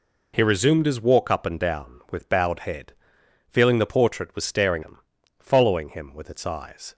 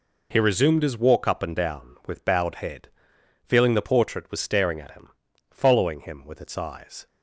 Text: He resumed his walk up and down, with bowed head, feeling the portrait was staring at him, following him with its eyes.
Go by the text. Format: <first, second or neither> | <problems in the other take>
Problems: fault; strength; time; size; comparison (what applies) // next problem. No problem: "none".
second | skips "at"; at 4.8 s